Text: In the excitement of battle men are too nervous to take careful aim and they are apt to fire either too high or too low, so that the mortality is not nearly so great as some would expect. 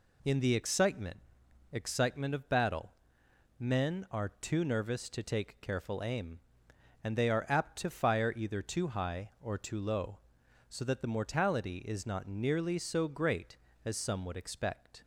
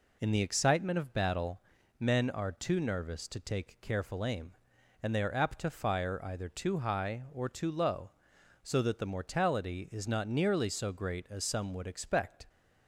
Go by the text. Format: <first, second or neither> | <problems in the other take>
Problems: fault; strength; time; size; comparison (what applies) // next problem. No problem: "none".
second | says "excitement" twice; at 1.7 s // pauses between "battle" and "men"; noticeable; at 2.9 s; 0.68 s long; also in the second